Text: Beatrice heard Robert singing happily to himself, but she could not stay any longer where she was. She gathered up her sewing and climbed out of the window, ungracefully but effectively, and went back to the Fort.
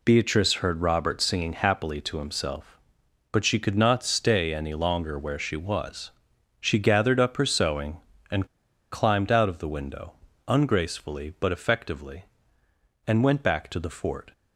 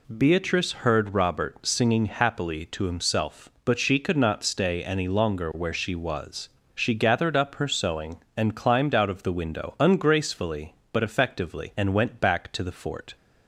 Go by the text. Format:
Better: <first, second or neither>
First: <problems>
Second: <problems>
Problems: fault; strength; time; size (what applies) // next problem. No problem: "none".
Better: second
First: pauses between "and" and "climbed"; noticeable; at 8.4 s; 0.46 s long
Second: none